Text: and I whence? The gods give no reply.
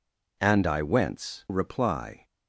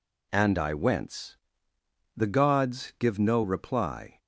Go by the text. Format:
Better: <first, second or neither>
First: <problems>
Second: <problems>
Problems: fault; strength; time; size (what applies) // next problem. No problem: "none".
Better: second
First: skips "The gods give no"; at 1.4 s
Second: none